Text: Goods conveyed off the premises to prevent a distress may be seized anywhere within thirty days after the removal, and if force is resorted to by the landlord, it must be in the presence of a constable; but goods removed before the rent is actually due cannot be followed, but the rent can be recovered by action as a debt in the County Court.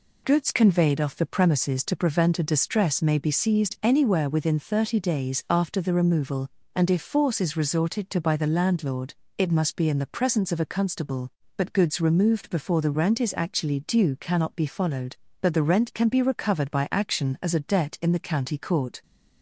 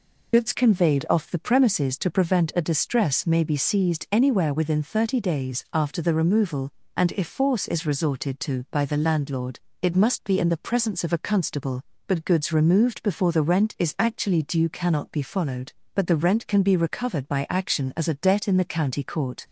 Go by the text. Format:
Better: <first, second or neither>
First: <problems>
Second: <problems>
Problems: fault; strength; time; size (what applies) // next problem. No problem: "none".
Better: first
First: none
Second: loses the start of "Goods"; at 0.3 s; 65 ms